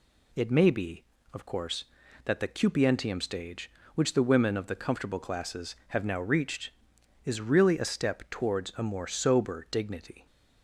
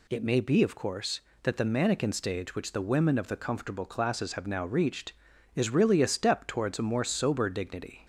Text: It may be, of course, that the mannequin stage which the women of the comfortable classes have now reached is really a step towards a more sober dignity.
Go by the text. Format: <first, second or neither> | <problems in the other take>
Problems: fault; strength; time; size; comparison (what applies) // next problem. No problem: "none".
second | says "cupientium" for "mannequin"; at 2.4 s